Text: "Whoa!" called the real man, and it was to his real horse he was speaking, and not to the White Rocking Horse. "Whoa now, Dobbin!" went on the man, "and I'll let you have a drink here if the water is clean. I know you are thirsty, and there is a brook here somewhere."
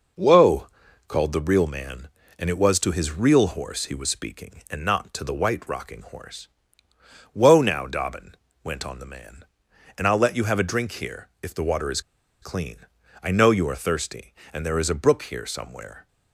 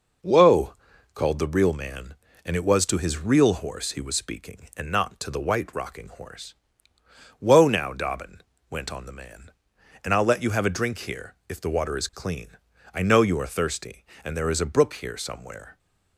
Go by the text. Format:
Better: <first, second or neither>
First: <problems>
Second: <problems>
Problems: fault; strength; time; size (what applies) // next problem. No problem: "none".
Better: second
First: pauses between "here" and "if"; slight; at 11.2 s; 0.16 s long // pauses between "is" and "clean"; at 11.9 s; 0.41 s long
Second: pauses between "here" and "if"; slight; at 11.3 s; 0.16 s long